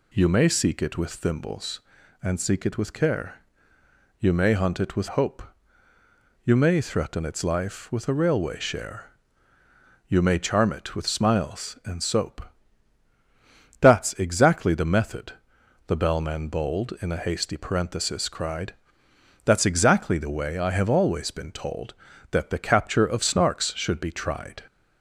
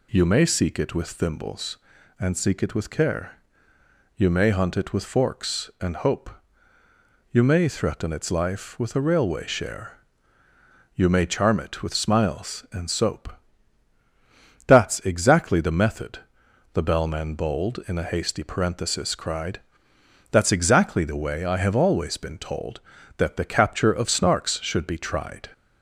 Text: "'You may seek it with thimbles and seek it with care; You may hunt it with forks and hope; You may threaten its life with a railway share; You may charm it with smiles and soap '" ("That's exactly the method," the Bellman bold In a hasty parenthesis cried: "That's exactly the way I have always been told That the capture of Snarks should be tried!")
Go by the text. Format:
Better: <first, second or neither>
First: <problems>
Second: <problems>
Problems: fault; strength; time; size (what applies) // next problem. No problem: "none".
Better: second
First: skips "forks and"; at 5.0 s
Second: none